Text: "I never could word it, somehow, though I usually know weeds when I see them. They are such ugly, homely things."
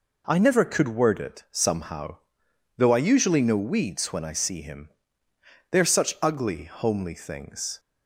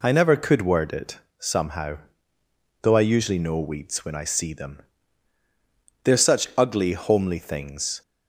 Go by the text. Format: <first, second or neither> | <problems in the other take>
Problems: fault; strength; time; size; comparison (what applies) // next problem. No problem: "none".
second | says "him" for "them"; at 4.6 s